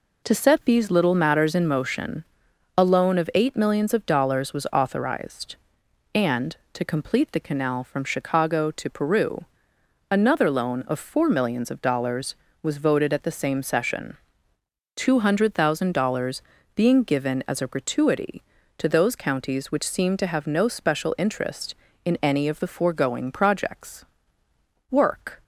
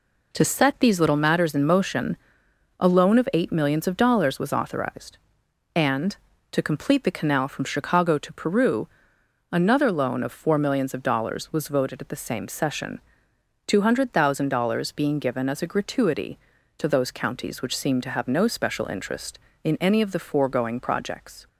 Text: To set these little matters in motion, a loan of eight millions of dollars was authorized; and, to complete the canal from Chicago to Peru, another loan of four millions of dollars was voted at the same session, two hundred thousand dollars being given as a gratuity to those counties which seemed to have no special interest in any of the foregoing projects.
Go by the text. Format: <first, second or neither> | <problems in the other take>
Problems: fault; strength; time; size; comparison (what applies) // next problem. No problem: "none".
second | pauses between "dollars" and "being"; slight; at 16.4 s; 0.36 s long // goes on to say "Work"; from 24.8 s on; 0.54 s long